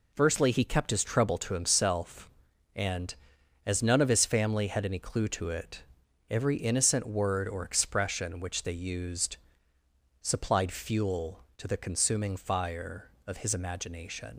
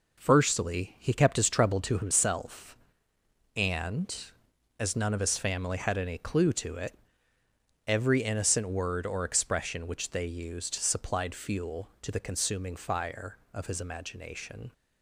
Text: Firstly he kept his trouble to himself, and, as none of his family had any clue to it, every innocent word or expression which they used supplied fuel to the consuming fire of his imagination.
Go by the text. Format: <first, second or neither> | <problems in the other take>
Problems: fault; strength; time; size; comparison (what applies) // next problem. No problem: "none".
second | pauses between "used" and "supplied"; noticeable; at 9.3 s; 0.84 s long // leaves "imagination" unfinished; at 14.3 s; 95 ms